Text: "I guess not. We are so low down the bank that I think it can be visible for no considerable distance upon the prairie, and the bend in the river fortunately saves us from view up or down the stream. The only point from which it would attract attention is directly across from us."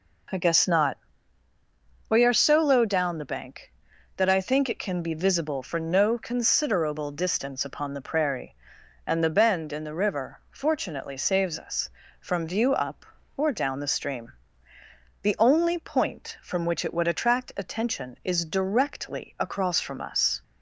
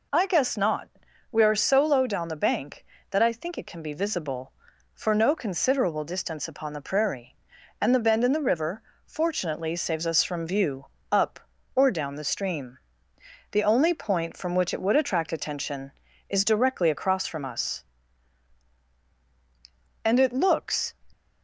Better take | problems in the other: first | pauses between "river" and "fortunately"; slight; at 8.8 s; 0.24 s long // pauses between "view" and "up"; slight; at 10.8 s; 0.24 s long // goes on to say "And it looks"; noticeable; from 20.0 s on; 0.92 s long

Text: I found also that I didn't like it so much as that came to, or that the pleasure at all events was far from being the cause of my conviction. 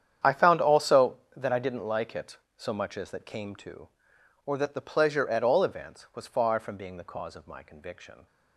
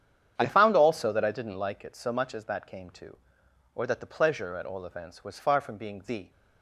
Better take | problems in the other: first | starts louder than the rest; strong; until 1.4 s; 8.5 dB; strong in the first // stops before "cause of my conviction"; at 6.2 s

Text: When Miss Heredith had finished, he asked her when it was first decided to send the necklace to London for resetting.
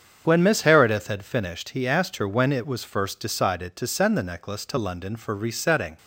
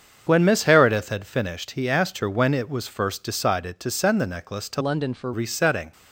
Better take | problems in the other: first | starts louder than the rest; until 1.2 s; 7 dB; strong in the first // changes voice from "London" to "for"; from 4.8 to 5.3 s; 0.5 s long

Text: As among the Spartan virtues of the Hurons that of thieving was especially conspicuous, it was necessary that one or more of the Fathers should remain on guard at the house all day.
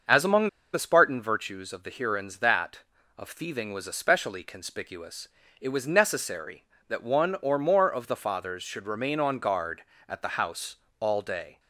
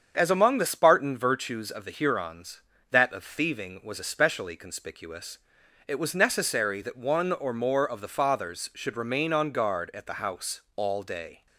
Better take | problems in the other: second | starts louder than the rest; until 1.3 s; 6.5 dB; strong in the second // pauses between "among" and "the"; slight; at 0.4 s; 0.26 s long // pauses between "house" and "all"; slight; at 10.7 s; 0.24 s long

